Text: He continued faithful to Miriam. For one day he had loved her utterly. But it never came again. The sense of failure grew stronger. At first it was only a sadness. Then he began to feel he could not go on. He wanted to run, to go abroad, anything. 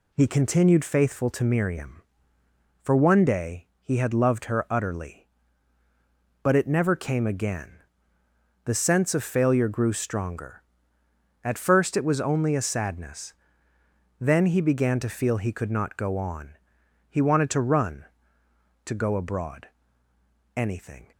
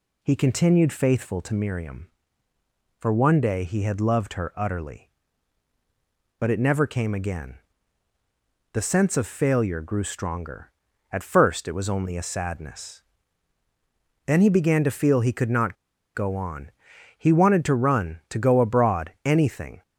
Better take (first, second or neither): first